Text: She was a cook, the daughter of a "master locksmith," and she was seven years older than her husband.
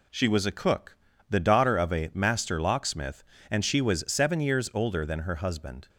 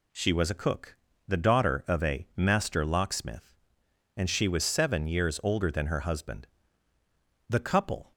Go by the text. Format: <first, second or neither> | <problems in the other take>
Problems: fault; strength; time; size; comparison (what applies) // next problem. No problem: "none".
first | goes on to say "The couple"; noticeable; from 7.4 s on; 0.64 s long